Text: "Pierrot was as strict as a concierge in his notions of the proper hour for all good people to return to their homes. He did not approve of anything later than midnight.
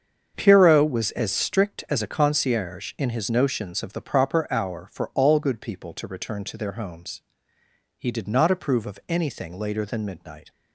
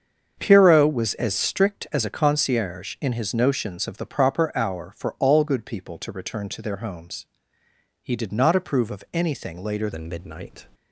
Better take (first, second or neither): first